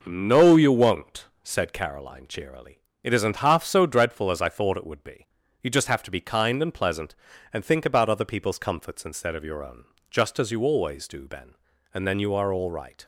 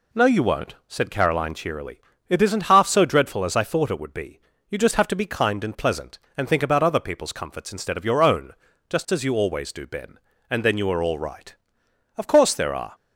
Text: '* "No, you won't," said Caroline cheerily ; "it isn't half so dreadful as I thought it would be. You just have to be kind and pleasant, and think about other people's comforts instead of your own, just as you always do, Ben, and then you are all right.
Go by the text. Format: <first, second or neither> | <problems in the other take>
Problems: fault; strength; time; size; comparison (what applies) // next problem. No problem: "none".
first | goes on to say "Of course there are"; noticeable; from 12.1 s on; 0.78 s long